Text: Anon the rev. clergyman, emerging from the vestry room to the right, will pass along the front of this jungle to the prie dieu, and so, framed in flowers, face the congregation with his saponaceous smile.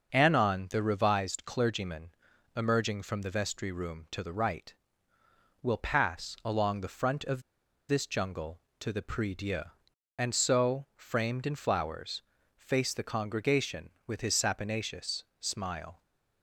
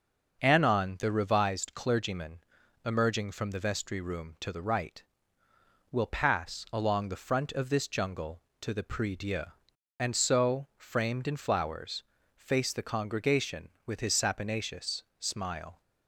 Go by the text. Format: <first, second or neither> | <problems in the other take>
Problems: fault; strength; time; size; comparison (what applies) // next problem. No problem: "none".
second | starts louder than the rest; noticeable; until 1.1 s; 6 dB; noticeable in the second // pauses between "of" and "this"; noticeable; at 7.4 s; 0.47 s long // pauses between "saponaceous" and "smile"; slight; at 15.2 s; 0.16 s long; slight in the second